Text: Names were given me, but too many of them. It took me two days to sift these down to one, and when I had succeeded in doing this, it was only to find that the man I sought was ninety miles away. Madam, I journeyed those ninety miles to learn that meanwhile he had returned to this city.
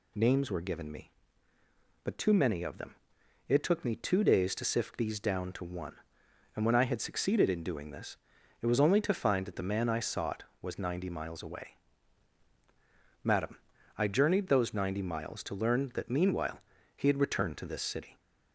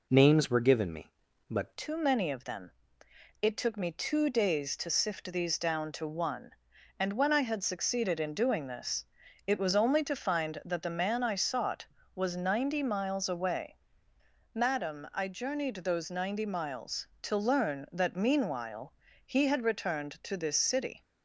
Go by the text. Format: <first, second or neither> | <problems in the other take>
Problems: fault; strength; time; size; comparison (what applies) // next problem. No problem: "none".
first | changes voice at "too"; from 1.7 s on; 19.3 s long // pauses between "meanwhile" and "he"; slight; at 18.9 s; 0.34 s long; slight in the first